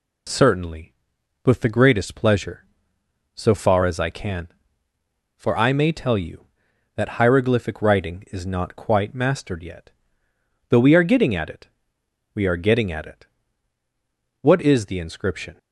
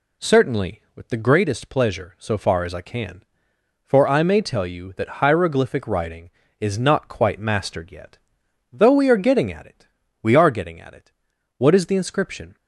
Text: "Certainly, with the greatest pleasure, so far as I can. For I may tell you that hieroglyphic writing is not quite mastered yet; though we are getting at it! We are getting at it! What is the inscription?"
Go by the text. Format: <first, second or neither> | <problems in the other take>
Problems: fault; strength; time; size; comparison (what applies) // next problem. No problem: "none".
neither | none